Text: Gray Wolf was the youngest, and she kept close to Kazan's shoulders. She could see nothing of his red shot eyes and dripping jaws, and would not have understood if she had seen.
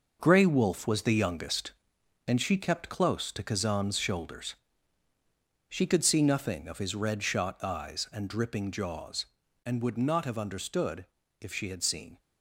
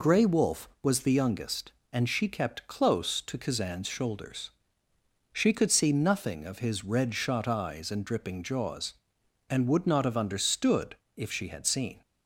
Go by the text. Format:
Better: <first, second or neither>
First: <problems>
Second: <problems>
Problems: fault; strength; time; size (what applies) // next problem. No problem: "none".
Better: second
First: gets quieter; strong; throughout; 8 dB // pauses between "understood" and "if"; slight; at 11.0 s; 0.34 s long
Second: pauses between "understood" and "if"; slight; at 10.9 s; 0.20 s long